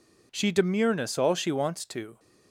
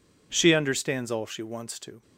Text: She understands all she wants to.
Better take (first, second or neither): second